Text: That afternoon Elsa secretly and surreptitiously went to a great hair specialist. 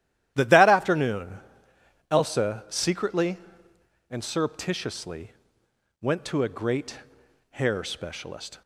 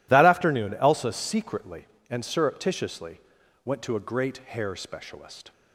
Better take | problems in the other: second | starts louder than the rest; strong; until 1.3 s; 12.5 dB // says "That" twice; at 0.4 s // pauses between "afternoon" and "Elsa"; noticeable; at 1.3 s; 0.70 s long // pauses between "surreptitiously" and "went"; noticeable; at 5.3 s; 0.70 s long; also in the second // pauses between "great" and "hair"; noticeable; at 6.9 s; 0.50 s long

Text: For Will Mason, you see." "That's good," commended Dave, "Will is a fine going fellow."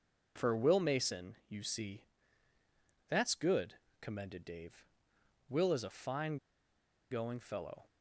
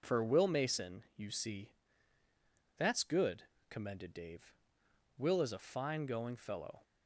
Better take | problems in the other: second | pauses between "fine" and "going"; noticeable; at 6.3 s; 0.74 s long

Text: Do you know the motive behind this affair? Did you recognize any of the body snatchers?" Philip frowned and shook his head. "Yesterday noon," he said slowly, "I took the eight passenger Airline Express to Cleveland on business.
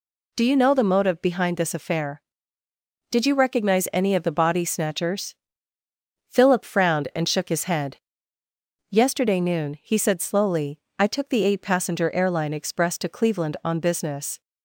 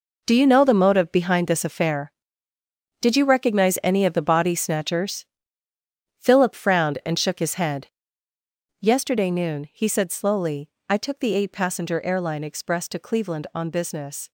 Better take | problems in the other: first | gets quieter; strong; throughout; 10 dB

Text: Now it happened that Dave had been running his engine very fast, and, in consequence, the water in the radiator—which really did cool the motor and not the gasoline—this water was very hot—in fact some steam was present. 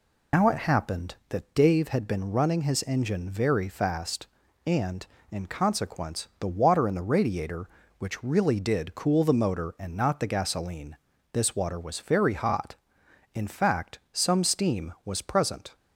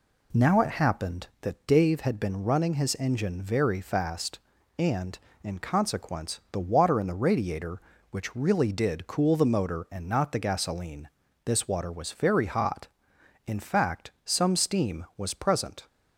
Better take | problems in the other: second | loses the start of "Now"; at 0.3 s; 150 ms

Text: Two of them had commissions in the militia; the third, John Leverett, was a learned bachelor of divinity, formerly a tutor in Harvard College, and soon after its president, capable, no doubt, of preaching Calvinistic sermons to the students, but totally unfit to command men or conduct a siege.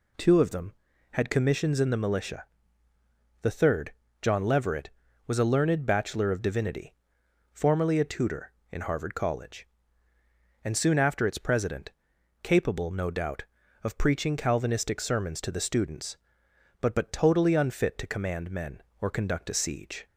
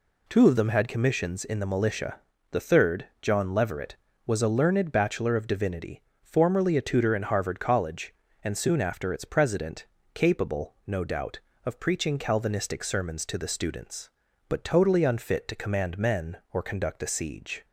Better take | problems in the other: second | says "but" twice; at 16.9 s

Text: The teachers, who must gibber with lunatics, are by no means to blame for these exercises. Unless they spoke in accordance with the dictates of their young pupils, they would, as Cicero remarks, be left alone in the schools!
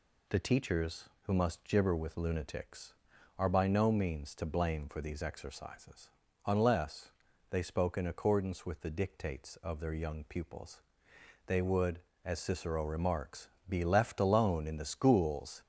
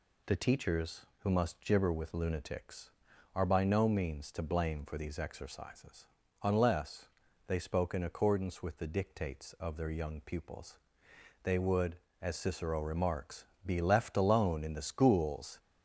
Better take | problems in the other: neither | pauses between "Unless" and "they"; the same in both

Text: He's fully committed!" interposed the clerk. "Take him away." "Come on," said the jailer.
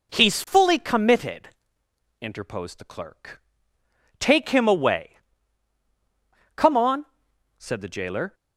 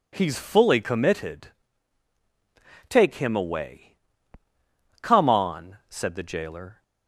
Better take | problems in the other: first | skips "interposed the clerk"; at 2.1 s

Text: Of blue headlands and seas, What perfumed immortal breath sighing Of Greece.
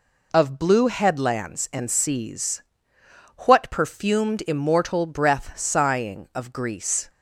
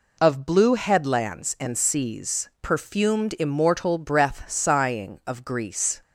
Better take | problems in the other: first | skips "What"; at 2.5 s

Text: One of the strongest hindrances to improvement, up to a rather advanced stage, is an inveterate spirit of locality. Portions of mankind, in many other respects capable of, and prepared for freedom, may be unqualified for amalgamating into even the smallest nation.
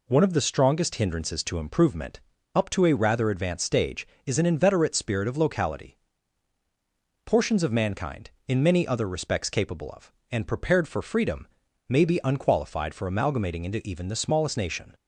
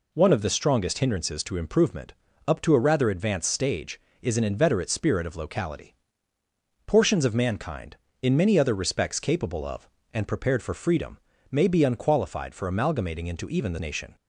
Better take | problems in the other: first | skips "smallest"; at 13.7 s

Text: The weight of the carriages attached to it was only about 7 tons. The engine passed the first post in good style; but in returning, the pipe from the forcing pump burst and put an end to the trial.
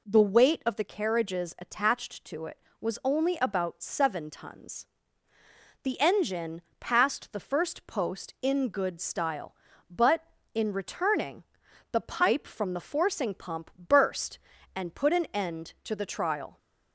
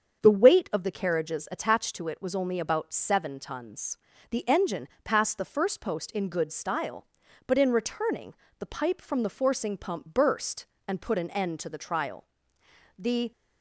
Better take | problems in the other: first | starts louder than the rest; strong; until 1.2 s; 7 dB // pauses between "engine" and "passed"; slight; at 4.8 s; 0.16 s long; slight in the first // goes on to say "The"; slight; from 12.9 s on; 0.34 s long

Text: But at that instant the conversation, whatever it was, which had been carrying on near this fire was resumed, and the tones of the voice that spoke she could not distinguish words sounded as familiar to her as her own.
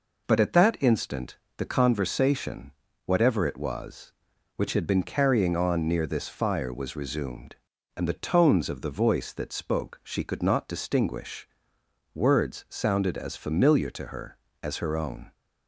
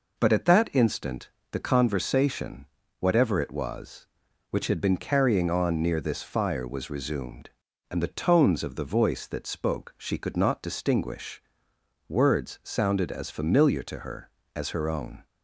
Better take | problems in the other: neither | pauses between "instant" and "the"; slight; the same in both // pauses between "distinguish" and "words"; noticeable; the same in both

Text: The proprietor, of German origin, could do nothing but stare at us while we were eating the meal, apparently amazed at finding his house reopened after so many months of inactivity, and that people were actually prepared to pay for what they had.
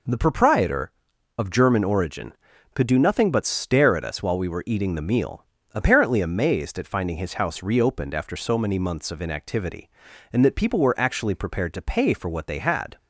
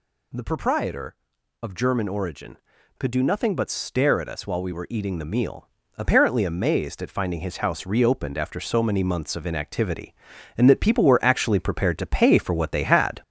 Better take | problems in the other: first | gets louder; throughout; 3.5 dB

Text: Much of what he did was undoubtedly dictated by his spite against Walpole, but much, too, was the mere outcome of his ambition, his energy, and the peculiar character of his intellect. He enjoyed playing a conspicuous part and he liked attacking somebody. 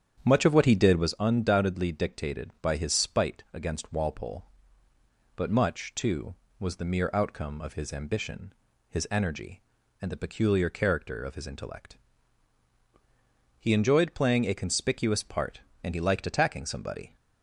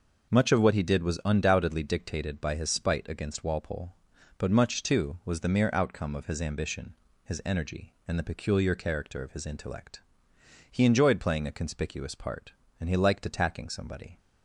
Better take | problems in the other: second | starts louder than the rest; strong; until 1.1 s; 8.5 dB

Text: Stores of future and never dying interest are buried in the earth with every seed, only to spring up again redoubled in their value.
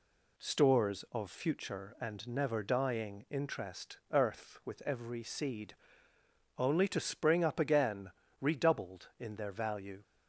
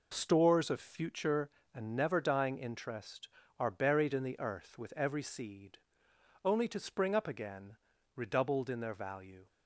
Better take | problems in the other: second | skips "are buried in the"; at 4.0 s // pauses between "again" and "redoubled"; slight; at 8.1 s; 0.32 s long; also in the second

